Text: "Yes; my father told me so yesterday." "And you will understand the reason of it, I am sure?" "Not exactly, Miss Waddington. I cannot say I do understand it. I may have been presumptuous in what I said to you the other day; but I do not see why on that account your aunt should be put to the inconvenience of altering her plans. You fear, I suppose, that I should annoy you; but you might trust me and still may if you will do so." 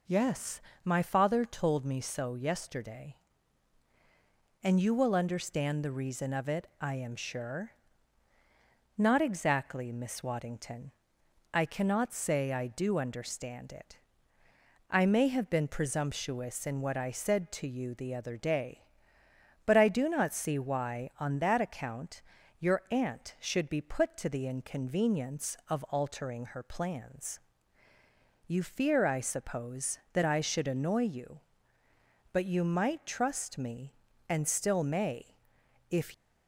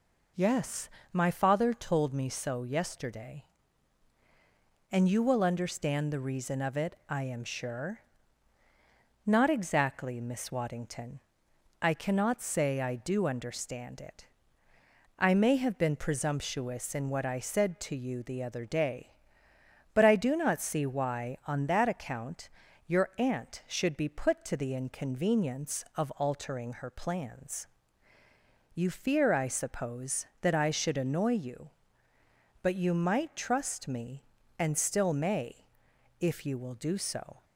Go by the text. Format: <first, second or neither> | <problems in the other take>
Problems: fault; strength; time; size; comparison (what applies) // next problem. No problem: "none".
second | pauses between "account" and "your"; at 22.2 s; 0.38 s long; also in the second // pauses between "may" and "if"; noticeable; at 35.3 s; 0.54 s long; noticeable in the second // stops before "you will do so"; at 36.1 s